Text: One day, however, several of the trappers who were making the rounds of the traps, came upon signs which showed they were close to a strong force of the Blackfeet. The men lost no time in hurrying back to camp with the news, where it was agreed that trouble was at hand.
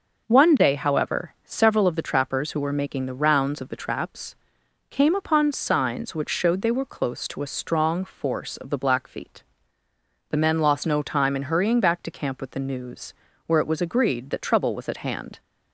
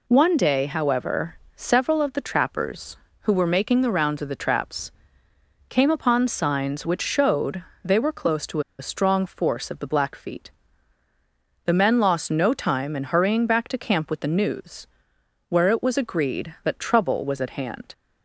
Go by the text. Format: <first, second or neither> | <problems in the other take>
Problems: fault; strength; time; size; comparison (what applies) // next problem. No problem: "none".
first | pauses between "showed" and "they"; slight; at 7.6 s; 0.18 s long // pauses between "to" and "a"; slight; at 8.6 s; 0.18 s long